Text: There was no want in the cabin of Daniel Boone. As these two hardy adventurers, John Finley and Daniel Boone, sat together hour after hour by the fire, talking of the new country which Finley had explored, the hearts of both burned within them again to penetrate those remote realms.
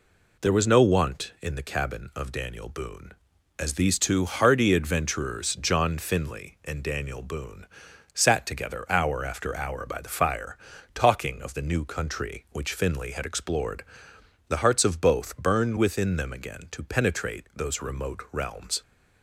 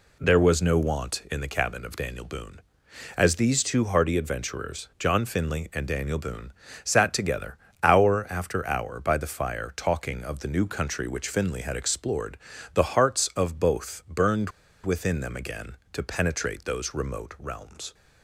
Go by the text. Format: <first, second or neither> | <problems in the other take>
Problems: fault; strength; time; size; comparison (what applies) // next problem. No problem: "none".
first | pauses between "together" and "hour"; slight; at 7.5 s; 0.26 s long // pauses between "burned" and "within"; slight; at 14.4 s; 0.34 s long